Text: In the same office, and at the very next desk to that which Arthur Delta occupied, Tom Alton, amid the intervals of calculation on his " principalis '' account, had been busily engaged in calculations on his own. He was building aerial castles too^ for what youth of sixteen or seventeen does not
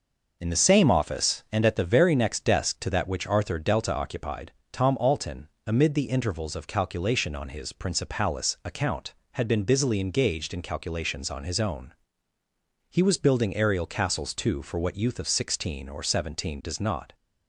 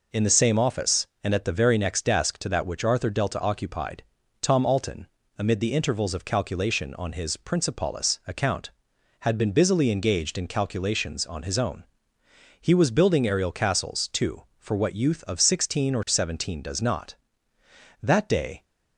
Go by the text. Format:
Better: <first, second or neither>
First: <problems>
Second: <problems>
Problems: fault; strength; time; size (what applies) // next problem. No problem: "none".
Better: first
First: none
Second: goes on to say "That day"; noticeable; from 18.0 s on; 0.62 s long